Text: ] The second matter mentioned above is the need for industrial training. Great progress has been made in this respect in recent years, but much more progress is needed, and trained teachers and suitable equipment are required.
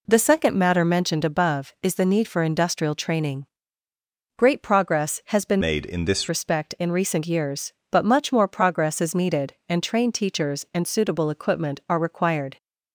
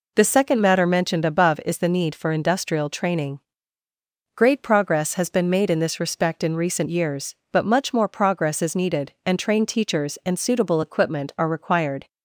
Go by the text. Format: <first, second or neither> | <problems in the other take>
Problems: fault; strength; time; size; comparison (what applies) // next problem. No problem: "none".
second | changes voice from "made" to "this"; from 5.6 to 6.2 s; 0.6 s long